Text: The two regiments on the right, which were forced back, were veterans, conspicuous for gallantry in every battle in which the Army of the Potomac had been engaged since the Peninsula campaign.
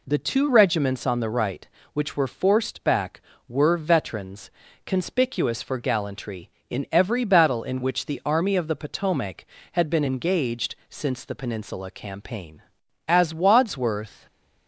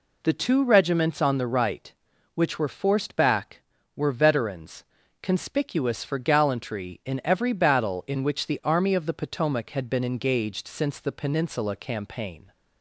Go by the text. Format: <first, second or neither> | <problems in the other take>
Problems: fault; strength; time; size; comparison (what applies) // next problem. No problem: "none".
second | pauses between "engaged" and "since"; slight; at 10.7 s; 0.16 s long // goes on to say "As Wadsworth"; noticeable; from 13.0 s on; 1.1 s long // stays silent after the last word; slight; from 14.1 s on; 0.5 s long